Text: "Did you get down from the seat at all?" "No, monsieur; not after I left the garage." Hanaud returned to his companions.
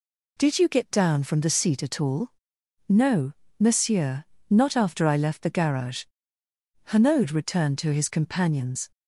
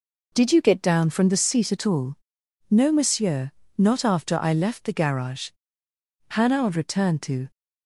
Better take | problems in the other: first | stops before "his companions"; at 7.5 s

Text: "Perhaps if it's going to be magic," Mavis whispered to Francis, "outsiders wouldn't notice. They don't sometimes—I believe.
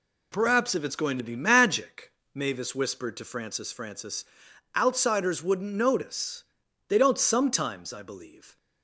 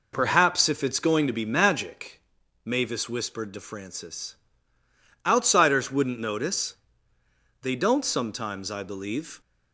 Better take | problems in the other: second | says "Francis" twice; at 3.7 s

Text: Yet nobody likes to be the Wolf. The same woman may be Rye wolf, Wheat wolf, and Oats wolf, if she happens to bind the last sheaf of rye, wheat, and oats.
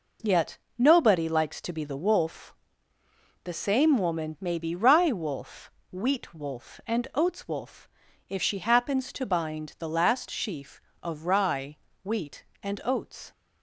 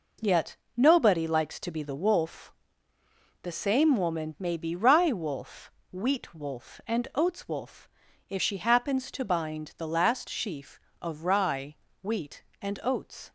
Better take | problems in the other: neither | pauses between "Yet" and "nobody"; slight; the same in both

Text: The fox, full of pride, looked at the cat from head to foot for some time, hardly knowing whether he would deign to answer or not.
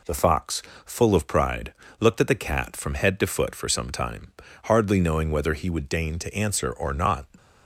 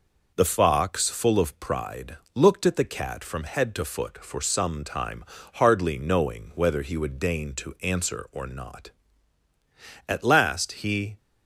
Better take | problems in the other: first | goes on to say "At last he"; noticeable; from 10.0 s on; 1.0 s long

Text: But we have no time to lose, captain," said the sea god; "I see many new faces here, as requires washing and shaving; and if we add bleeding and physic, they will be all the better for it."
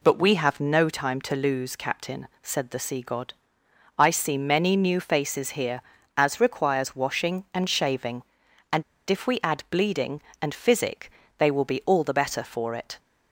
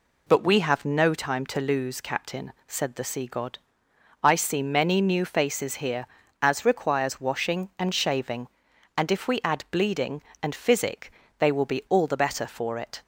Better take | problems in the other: second | pauses between "and" and "if"; slight; at 8.8 s; 0.25 s long

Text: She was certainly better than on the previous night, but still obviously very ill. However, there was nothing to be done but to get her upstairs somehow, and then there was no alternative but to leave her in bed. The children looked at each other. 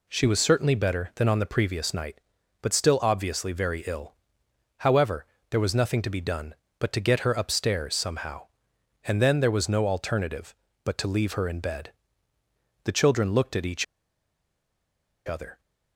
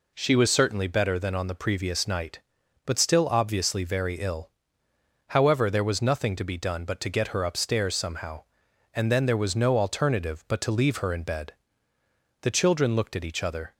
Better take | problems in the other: second | pauses between "each" and "other"; strong; at 13.8 s; 1.4 s long

